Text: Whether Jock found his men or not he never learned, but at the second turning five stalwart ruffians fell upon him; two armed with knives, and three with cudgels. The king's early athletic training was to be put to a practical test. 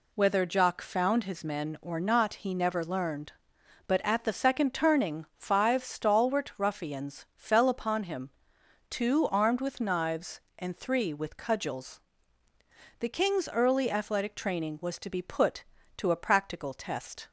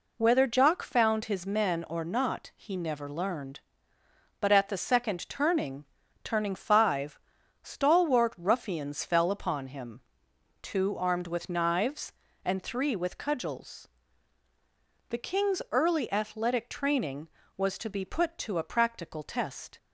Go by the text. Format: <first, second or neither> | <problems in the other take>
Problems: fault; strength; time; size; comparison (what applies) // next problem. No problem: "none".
first | says "turning" twice; at 6.2 s // pauses between "five" and "stalwart"; at 7.1 s; 0.44 s long